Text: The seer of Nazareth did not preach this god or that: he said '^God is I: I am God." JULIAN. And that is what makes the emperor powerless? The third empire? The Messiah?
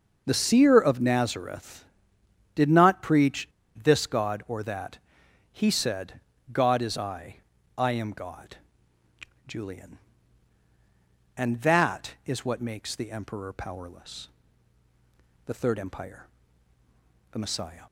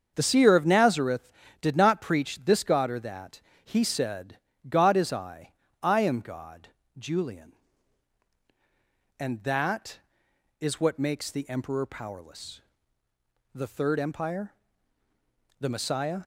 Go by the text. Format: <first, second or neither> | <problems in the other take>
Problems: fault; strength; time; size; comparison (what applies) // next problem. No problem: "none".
second | starts louder than the rest; until 1.2 s; 6 dB; also in the second // pauses between "preach" and "this"; slight; at 3.4 s; 0.33 s long // pauses between "said" and "God"; slight; at 6.2 s; 0.32 s long; slight in the second